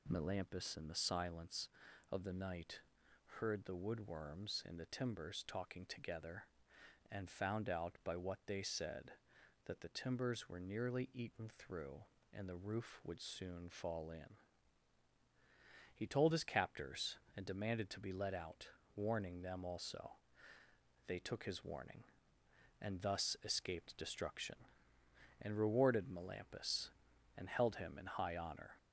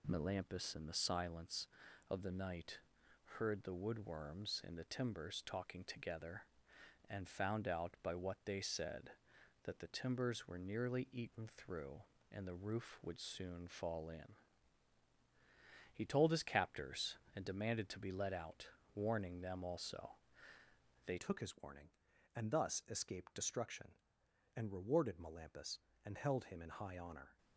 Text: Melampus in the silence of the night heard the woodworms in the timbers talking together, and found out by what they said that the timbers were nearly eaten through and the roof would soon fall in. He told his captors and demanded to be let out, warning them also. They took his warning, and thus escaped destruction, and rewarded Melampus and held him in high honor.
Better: first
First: pauses between "night" and "heard"; noticeable; at 2.8 s; 0.58 s long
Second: pauses between "night" and "heard"; noticeable; at 2.7 s; 0.58 s long // changes voice at "took"; from 21.1 s on; 6.2 s long

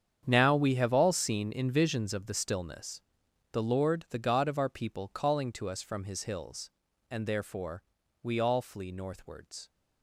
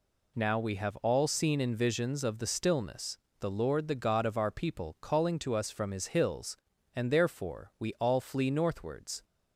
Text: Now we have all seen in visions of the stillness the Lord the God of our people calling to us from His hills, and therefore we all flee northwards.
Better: second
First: gets quieter; strong; throughout; 14.5 dB // pauses between "stillness" and "the"; noticeable; at 3.0 s; 0.50 s long // pauses between "therefore" and "we"; at 7.8 s; 0.40 s long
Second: pauses between "stillness" and "the"; slight; at 3.1 s; 0.22 s long

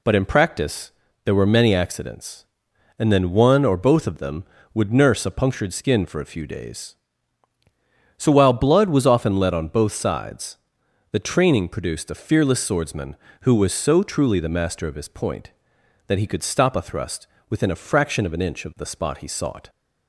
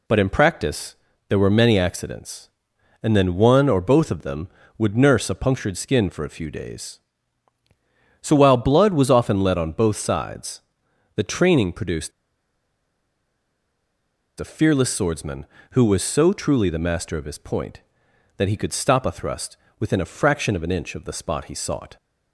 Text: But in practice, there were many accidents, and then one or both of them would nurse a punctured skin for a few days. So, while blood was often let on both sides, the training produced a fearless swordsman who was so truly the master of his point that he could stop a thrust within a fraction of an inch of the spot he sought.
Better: first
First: pauses between "thrust" and "within"; slight; at 17.2 s; 0.22 s long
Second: pauses between "produced" and "a"; strong; at 12.1 s; 2.2 s long // pauses between "thrust" and "within"; slight; at 19.5 s; 0.22 s long

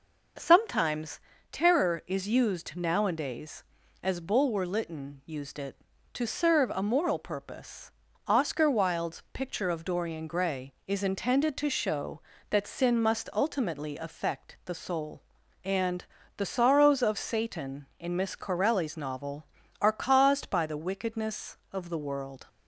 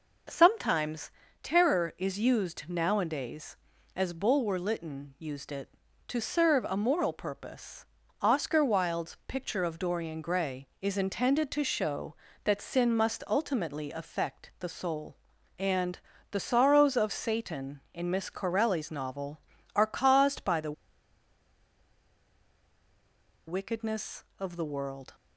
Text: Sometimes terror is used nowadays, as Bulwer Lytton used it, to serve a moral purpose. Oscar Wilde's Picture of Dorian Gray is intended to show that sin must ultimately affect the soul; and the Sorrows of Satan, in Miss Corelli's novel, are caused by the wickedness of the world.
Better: first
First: pauses between "Sometimes" and "terror"; slight; at 1.1 s; 0.32 s long // pauses between "and" and "the"; slight; at 16.0 s; 0.32 s long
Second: pauses between "Sometimes" and "terror"; slight; at 1.1 s; 0.32 s long // pauses between "and" and "the"; slight; at 15.9 s; 0.32 s long // pauses between "the" and "wickedness"; strong; at 20.7 s; 2.7 s long

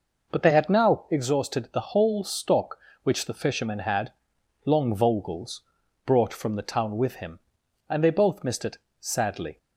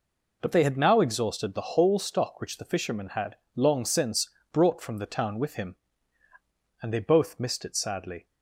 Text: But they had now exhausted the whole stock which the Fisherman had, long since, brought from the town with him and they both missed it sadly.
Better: second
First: says "vogels" for "since"; at 4.9 s // pauses between "it" and "sadly"; slight; at 8.7 s; 0.20 s long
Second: none

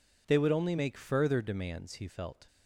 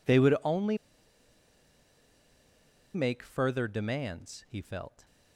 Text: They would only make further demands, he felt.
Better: first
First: none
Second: pauses between "only" and "make"; strong; at 0.7 s; 2.1 s long

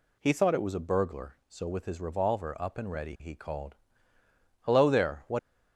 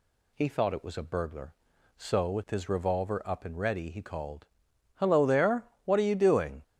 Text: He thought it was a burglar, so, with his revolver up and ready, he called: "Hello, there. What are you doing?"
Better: second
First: stops before "are you doing"; at 5.3 s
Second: none

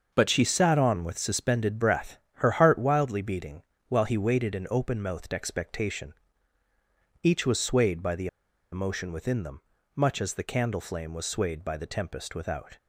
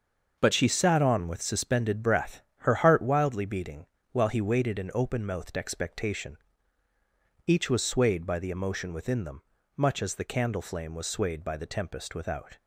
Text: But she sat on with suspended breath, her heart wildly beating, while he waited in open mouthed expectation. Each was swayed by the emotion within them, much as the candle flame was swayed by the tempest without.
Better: second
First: starts louder than the rest; until 1.1 s; 6.5 dB // pauses between "the" and "emotion"; at 8.2 s; 0.45 s long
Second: starts louder than the rest; until 1.4 s; 6.5 dB

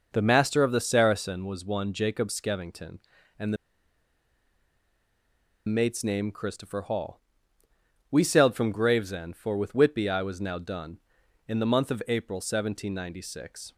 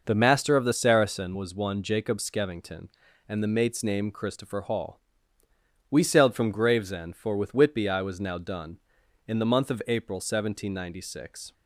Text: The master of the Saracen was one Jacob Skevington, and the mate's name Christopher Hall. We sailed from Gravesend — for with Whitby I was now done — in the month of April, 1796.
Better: second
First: pauses between "the" and "mate's"; strong; at 3.5 s; 2.1 s long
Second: none

